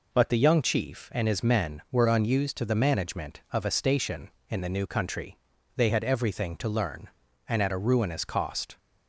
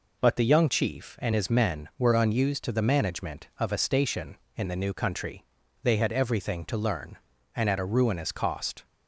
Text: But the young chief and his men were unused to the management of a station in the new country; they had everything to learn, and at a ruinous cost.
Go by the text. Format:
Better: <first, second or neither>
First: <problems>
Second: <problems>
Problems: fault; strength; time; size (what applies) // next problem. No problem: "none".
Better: neither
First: none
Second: none